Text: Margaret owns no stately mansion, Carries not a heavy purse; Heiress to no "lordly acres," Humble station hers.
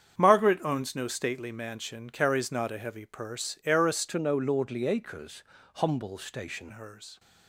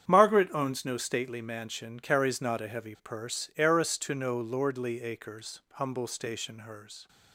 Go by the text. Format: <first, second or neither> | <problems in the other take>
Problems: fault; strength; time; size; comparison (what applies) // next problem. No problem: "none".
second | starts louder than the rest; strong; until 1.2 s; 7.5 dB; strong in the second // changes voice from "to" to "station"; from 4.0 to 6.7 s; 2.7 s long